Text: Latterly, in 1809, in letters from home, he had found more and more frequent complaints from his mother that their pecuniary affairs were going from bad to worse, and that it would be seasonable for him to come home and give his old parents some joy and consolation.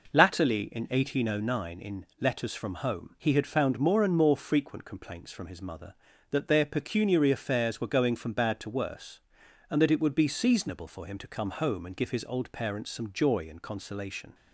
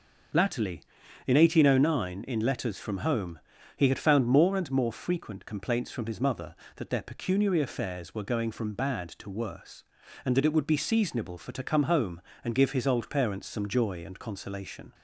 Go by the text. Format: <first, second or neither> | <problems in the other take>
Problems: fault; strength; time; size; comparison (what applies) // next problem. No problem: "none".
first | starts louder than the rest; until 1.7 s; 6.5 dB // skips "him"; at 11.5 s